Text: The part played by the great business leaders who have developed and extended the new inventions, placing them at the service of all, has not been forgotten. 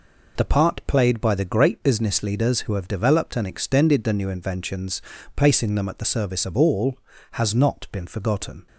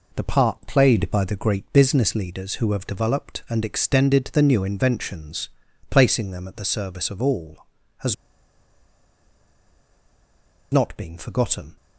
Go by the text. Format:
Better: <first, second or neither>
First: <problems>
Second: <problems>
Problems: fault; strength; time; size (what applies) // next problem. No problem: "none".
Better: first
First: none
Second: pauses between "has" and "not"; strong; at 8.1 s; 2.5 s long